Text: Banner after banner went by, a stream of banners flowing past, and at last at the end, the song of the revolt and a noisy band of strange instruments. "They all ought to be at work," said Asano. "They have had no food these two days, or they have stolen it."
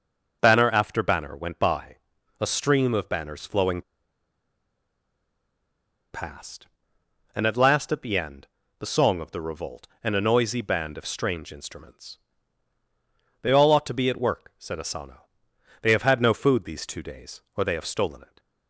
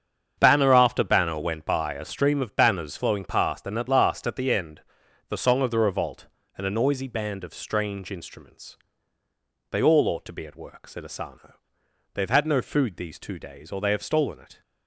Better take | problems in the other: second | starts louder than the rest; noticeable; until 1.4 s; 6 dB; strong in the second // pauses between "flowing" and "past"; strong; at 3.8 s; 2.3 s long

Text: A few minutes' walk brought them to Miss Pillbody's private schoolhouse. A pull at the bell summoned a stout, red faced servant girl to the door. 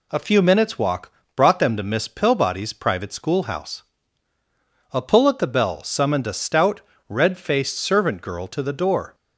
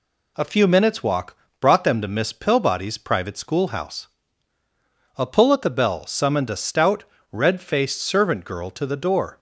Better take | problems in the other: neither | pauses between "walk" and "brought"; slight; the same in both

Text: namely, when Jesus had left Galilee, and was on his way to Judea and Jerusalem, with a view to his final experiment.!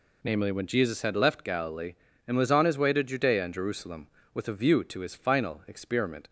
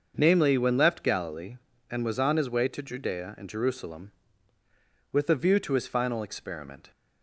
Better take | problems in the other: first | starts louder than the rest; until 1.1 s; 6.5 dB // skips "Jesus had"; at 0.7 s

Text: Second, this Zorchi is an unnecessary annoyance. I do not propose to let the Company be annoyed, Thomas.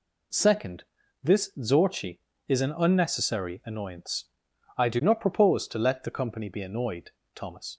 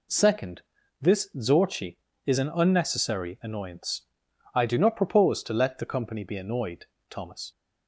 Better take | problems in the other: neither | none

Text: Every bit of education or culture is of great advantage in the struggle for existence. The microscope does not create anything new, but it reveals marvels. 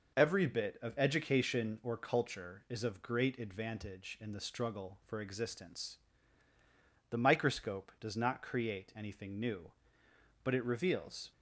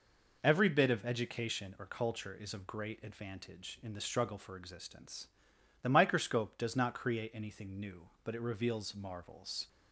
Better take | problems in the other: second | stops before "marvels"; at 11.3 s

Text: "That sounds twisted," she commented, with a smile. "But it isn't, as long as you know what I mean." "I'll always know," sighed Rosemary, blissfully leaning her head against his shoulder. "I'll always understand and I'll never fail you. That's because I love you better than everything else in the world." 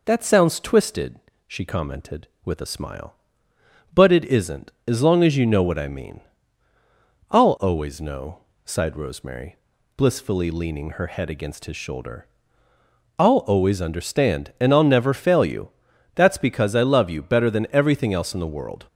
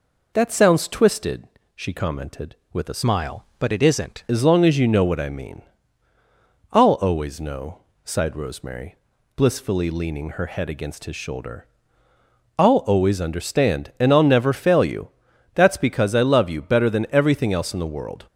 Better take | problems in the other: first | changes voice from "smile" to "isn't"; from 3.0 to 4.2 s; 1.2 s long

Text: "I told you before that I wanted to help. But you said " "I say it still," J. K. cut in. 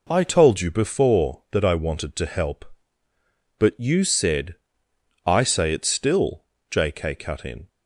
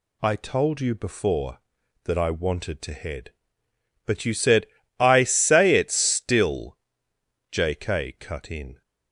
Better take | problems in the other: first | says "head" for "help"; at 2.9 s

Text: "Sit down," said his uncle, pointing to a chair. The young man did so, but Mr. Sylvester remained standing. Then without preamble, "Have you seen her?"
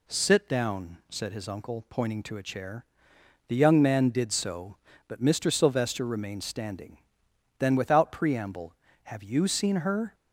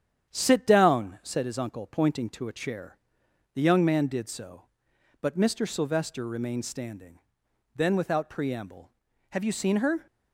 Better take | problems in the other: first | gets quieter; slight; throughout; 3 dB

